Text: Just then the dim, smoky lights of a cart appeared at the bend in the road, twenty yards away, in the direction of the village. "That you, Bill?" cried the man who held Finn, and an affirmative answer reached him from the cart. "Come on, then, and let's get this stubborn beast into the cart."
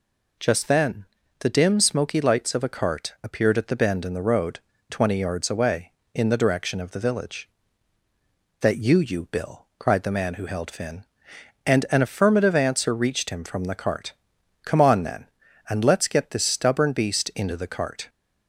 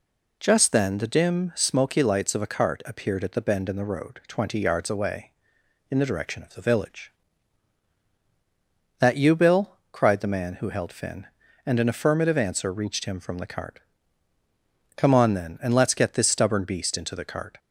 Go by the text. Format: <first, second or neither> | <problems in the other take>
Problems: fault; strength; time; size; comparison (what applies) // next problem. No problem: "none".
second | pauses between "then" and "the"; slight; at 1.0 s; 0.34 s long // says "you" twice; at 8.9 s